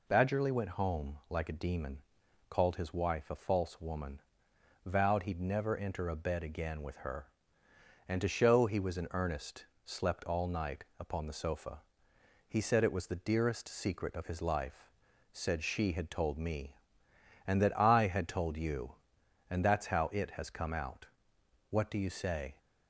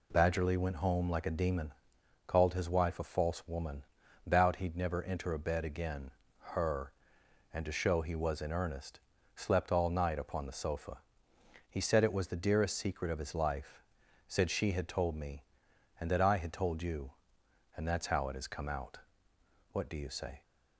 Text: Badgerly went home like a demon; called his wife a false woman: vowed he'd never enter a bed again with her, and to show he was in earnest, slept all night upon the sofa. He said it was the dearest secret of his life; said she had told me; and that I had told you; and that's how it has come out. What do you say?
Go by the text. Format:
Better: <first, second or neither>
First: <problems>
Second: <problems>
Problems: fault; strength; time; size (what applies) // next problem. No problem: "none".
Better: first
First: none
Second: skips "with"; at 6.2 s